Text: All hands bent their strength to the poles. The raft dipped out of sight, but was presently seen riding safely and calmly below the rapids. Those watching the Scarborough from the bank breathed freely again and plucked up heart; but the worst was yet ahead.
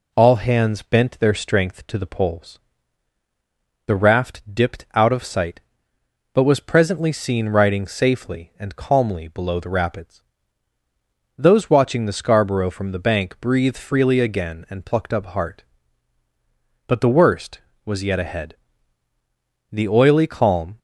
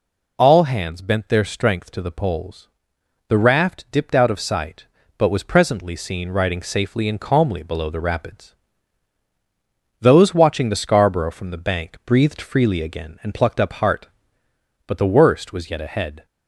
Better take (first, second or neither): second